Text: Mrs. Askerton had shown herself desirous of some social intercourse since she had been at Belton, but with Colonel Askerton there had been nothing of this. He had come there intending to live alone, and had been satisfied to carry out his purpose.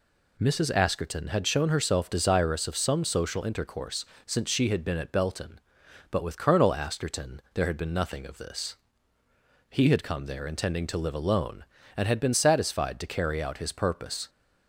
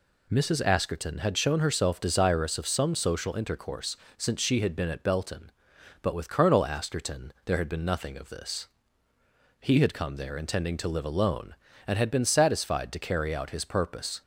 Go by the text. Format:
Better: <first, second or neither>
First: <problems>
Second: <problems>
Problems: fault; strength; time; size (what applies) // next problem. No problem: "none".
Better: neither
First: pauses between "intercourse" and "since"; slight; at 4.0 s; 0.20 s long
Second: pauses between "intercourse" and "since"; slight; at 3.9 s; 0.20 s long